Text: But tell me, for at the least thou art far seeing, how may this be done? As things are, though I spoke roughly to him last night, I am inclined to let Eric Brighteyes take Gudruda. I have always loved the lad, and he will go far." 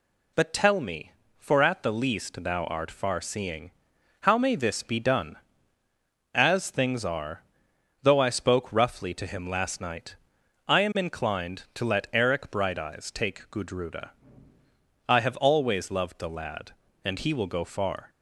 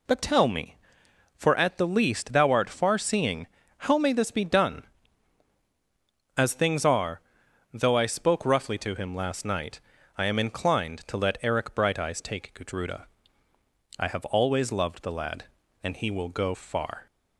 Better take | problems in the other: neither | none

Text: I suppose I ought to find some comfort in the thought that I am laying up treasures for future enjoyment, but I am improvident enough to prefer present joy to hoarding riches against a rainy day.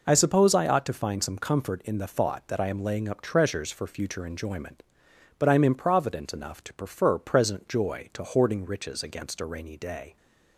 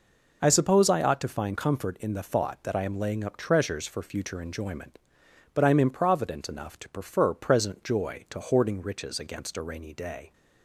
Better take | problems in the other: first | skips "some"; at 1.5 s

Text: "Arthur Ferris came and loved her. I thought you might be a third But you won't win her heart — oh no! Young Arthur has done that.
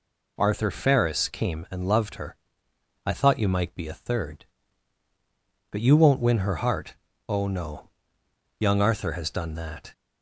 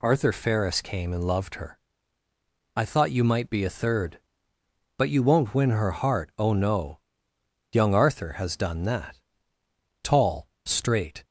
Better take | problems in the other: first | goes on to say "Tall straight"; noticeable; from 10.0 s on; 1.2 s long

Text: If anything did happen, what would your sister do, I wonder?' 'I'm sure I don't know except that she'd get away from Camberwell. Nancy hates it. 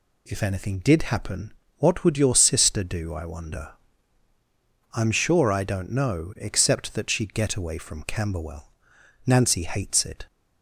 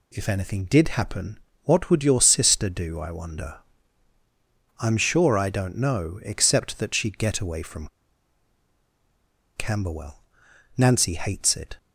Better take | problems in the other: first | pauses between "from" and "Camberwell"; strong; at 7.8 s; 1.6 s long

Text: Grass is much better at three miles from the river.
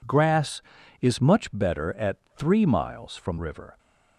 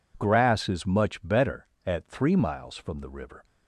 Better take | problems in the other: second | pauses between "at" and "three"; slight; at 2.1 s; 0.20 s long // skips "the"; at 3.3 s

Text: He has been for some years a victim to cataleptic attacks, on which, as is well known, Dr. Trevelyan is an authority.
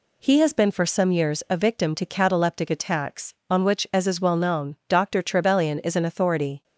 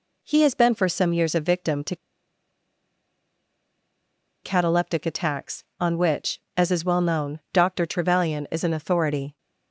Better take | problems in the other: first | pauses between "to" and "cataleptic"; strong; at 1.9 s; 2.4 s long

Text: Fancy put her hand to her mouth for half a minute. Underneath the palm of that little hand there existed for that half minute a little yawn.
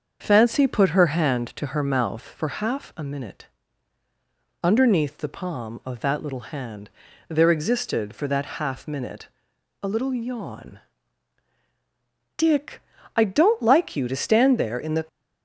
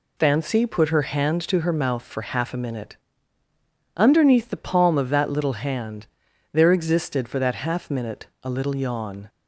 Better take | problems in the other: second | starts louder than the rest; until 1.2 s; 6.5 dB // pauses between "hand" and "there"; slight; at 6.9 s; 0.36 s long; noticeable in the second // pauses between "minute" and "a"; noticeable; at 9.2 s; 0.52 s long // goes on to say "Dick I don't like you to stand there in the"; strong; from 12.3 s on; 2.7 s long

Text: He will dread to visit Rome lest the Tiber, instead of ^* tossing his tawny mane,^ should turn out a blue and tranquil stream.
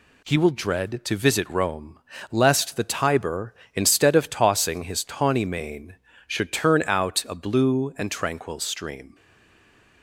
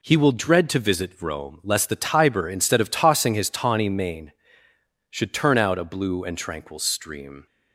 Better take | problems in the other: second | pauses between "Rome" and "lest"; slight; at 1.9 s; 0.32 s long // stays silent after the last word; slight; from 9.1 s on; 0.9 s long

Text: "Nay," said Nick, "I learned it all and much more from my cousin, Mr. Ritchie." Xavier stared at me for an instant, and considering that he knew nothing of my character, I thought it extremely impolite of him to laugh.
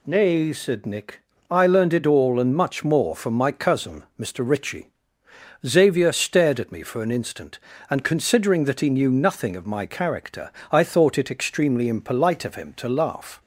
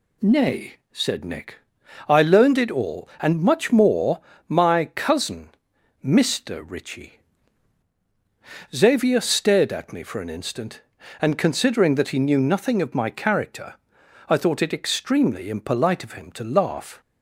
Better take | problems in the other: first | skips "from"; at 4.3 s

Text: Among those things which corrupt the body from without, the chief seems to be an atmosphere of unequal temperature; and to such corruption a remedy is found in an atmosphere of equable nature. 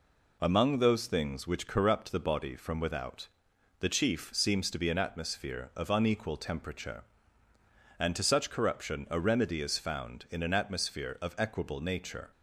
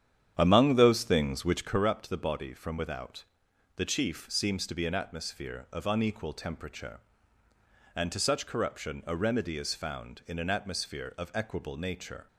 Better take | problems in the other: first | starts louder than the rest; strong; until 1.8 s; 9 dB

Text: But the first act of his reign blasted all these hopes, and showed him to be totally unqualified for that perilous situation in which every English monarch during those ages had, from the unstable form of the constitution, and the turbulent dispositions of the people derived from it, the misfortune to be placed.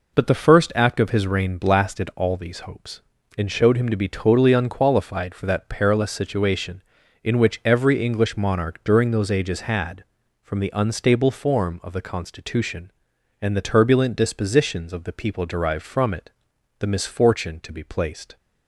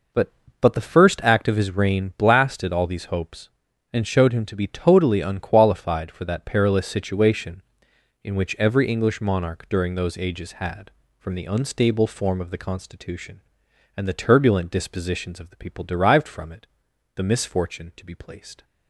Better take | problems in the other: first | says "But" twice; at 0.6 s

